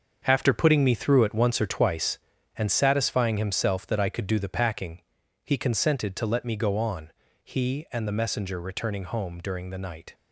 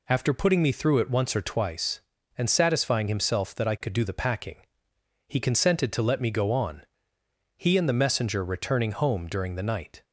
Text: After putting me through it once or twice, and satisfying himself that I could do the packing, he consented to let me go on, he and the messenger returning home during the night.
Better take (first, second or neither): second